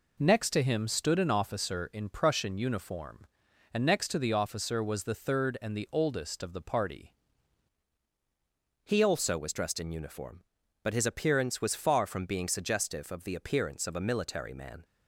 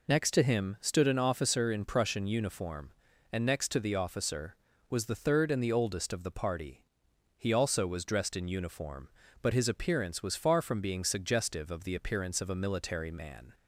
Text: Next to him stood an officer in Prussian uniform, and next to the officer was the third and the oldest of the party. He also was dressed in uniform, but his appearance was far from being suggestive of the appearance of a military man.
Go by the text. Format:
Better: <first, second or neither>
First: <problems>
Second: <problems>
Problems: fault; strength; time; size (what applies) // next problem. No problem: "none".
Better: second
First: changes voice at "He"; from 8.8 s on; 6.0 s long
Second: none